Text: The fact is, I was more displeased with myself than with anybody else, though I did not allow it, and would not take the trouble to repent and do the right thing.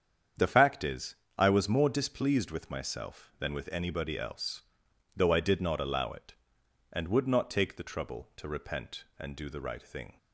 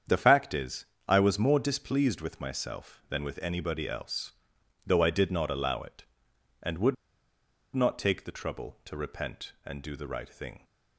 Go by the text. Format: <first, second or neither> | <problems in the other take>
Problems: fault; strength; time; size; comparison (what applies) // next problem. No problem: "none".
first | starts louder than the rest; strong; until 1.3 s; 8 dB; strong in the first // pauses between "would" and "not"; noticeable; at 6.9 s; 0.78 s long